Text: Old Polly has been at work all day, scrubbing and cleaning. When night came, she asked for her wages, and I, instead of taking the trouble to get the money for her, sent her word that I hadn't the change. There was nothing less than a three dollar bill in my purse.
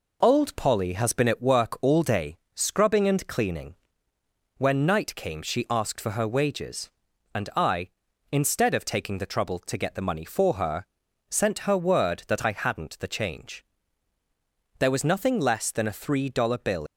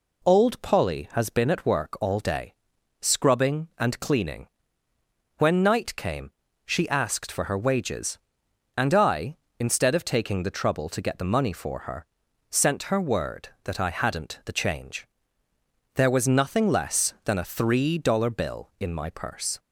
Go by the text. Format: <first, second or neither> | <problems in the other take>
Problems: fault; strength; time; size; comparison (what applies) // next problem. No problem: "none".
second | stops before "in my purse"; at 16.8 s